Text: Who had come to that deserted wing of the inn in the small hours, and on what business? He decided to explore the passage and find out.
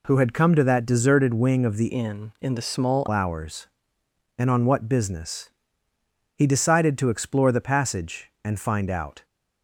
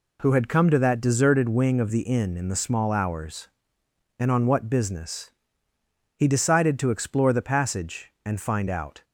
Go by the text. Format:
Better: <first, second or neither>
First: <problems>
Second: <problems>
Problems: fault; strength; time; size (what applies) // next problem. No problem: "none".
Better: second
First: changes voice from "inn" to "small"; from 1.8 to 3.0 s; 1.2 s long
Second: none